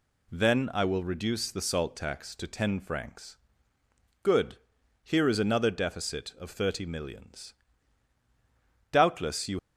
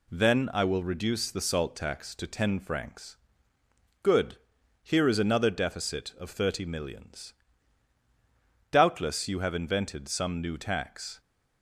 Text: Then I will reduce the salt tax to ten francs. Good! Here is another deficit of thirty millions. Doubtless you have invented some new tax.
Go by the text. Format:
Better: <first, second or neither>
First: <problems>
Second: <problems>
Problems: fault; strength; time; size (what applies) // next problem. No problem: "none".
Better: second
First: stops before "have invented some new tax"; at 9.5 s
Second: none